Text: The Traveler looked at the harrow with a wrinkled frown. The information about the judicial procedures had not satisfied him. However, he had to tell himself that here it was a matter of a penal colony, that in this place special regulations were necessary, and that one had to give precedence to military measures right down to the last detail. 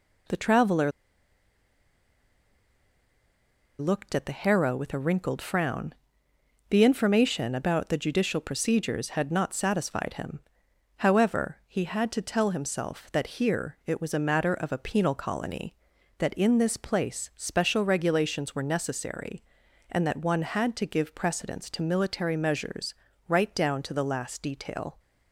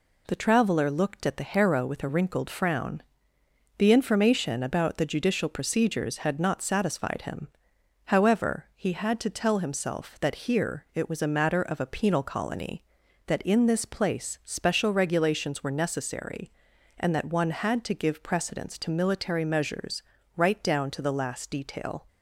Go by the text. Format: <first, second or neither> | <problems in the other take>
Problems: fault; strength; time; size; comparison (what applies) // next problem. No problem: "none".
second | pauses between "Traveler" and "looked"; strong; at 0.9 s; 2.8 s long // pauses between "measures" and "right"; slight; at 22.9 s; 0.34 s long; slight in the second